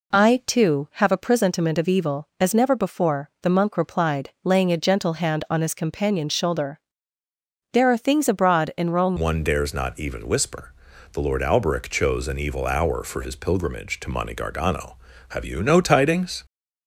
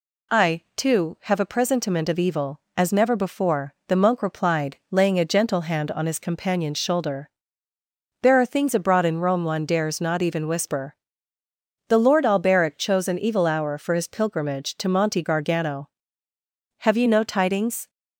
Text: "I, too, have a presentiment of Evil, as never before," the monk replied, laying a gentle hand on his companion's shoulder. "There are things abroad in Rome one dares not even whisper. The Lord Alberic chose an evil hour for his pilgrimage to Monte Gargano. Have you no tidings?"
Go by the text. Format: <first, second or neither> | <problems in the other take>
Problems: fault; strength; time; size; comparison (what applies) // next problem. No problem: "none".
second | changes voice at "one"; from 9.1 s on; 7.3 s long